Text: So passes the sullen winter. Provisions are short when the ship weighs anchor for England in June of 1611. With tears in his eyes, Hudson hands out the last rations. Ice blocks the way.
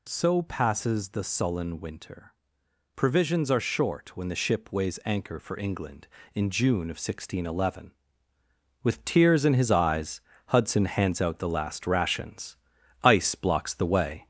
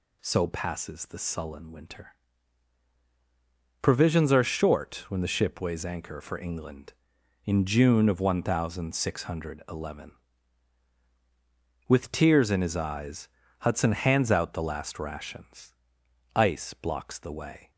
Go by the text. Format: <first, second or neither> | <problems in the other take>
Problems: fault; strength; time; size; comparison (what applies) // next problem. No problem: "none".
second | gets louder; slight; throughout; 2.5 dB